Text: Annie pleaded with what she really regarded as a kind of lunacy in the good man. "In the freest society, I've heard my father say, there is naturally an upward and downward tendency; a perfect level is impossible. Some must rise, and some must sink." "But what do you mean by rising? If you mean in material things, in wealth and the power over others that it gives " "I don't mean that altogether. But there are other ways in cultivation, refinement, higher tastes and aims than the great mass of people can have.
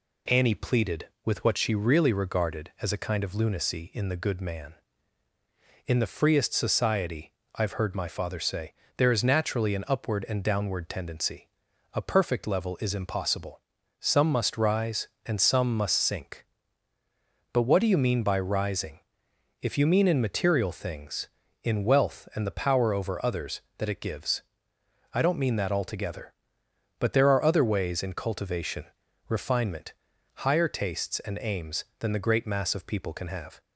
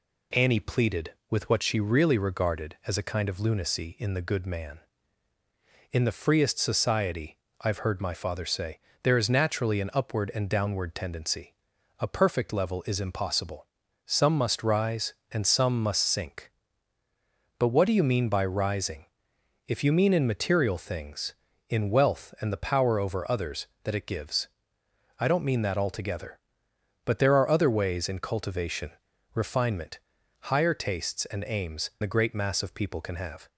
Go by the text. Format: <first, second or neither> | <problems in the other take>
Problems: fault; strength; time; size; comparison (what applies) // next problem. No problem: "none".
first | skips "than"; at 31.9 s